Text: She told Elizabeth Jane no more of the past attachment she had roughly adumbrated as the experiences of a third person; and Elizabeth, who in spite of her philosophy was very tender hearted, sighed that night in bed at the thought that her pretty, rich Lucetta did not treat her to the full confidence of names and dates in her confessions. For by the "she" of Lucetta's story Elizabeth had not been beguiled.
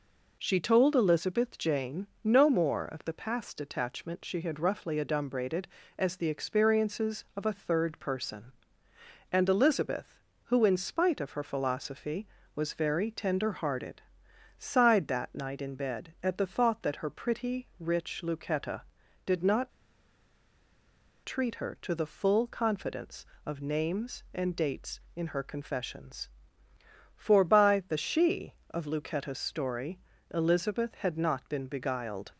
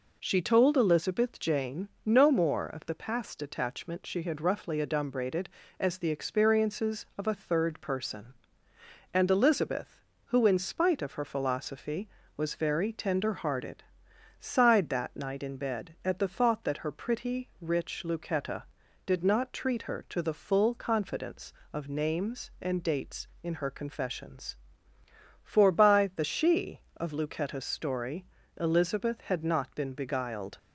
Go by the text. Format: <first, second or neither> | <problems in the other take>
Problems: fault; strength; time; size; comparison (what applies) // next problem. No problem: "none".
second | pauses between "Jane" and "no"; slight; at 2.0 s; 0.16 s long; slight in the second // pauses between "not" and "treat"; strong; at 19.7 s; 1.5 s long // pauses between "story" and "Elizabeth"; slight; at 29.9 s; 0.34 s long; slight in the second